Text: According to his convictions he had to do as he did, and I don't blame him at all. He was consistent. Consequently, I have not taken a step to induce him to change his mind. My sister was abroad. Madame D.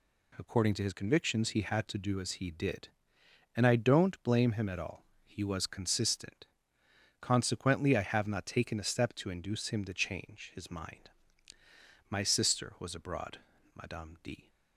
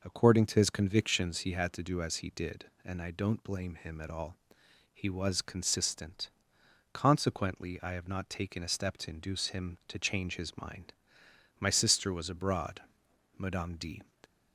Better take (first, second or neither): neither